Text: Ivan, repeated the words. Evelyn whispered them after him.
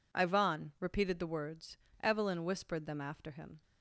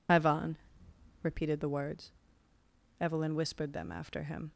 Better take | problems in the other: first | loses the start of "Ivan"; at 0.0 s; 45 ms

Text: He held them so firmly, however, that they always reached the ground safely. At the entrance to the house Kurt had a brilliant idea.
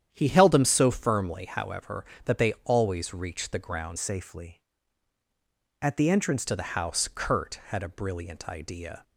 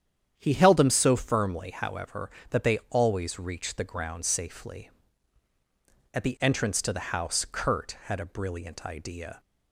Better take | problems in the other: second | starts louder than the rest; strong; until 1.1 s; 9.5 dB; strong in the second // changes voice from "safely" to "entrance"; from 3.9 to 6.4 s; 2.5 s long

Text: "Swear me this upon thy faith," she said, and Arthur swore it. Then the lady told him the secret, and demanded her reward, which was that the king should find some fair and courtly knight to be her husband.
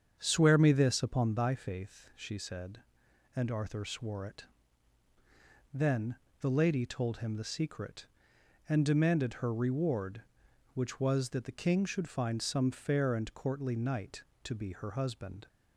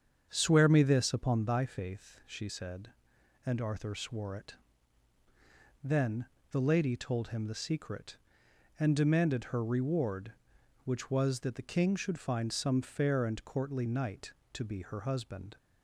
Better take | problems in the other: neither | starts louder than the rest; strong; the same in both // pauses between "Then" and "the"; slight; the same in both

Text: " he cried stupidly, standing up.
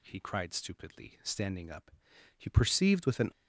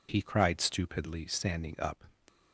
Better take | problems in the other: second | goes on to say "He perceived with an"; noticeable; from 2.3 s on; 0.92 s long

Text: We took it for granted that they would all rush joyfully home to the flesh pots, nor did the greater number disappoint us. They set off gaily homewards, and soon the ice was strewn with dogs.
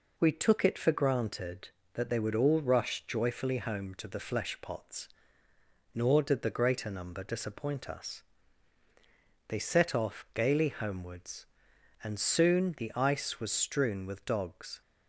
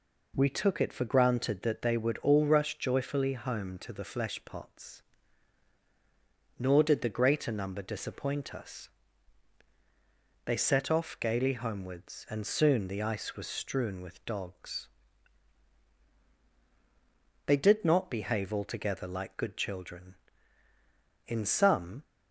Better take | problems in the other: first | goes on to say "They did not behave altogether like good children In some"; strong; from 17.4 s on; 4.5 s long

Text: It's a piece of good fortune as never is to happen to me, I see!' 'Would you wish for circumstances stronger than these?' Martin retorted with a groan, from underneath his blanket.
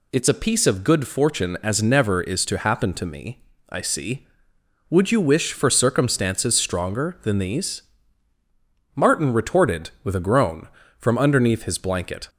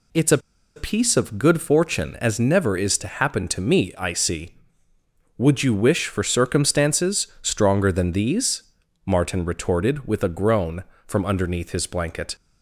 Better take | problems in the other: first | pauses between "a" and "piece"; at 0.3 s; 0.37 s long // pauses between "circumstances" and "stronger"; slight; at 7.2 s; 0.16 s long

